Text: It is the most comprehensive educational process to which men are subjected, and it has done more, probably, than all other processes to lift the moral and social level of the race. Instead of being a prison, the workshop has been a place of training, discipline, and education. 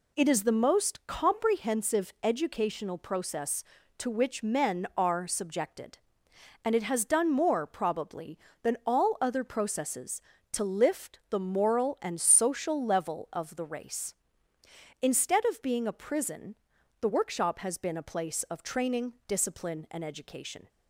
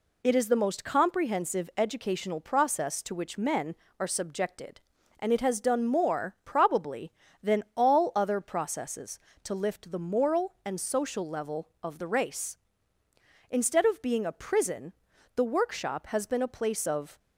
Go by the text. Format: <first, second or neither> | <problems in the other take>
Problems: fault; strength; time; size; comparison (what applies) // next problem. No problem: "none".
first | stops before "training discipline and education"; at 17.1 s